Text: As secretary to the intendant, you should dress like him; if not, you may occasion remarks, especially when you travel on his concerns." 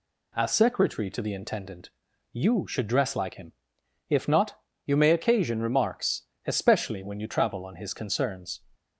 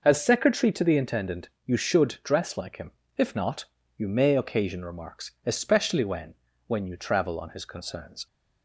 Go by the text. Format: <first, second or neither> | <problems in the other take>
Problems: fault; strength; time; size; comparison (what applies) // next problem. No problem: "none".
first | says "when" twice; at 6.6 s